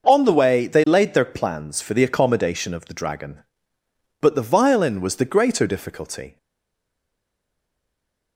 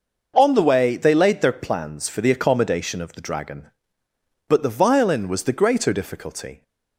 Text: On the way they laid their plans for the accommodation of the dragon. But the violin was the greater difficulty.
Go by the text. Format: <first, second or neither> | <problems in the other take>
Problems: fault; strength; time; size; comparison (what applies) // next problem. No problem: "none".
second | stays silent after the last word; noticeable; from 6.3 s on; 2.0 s long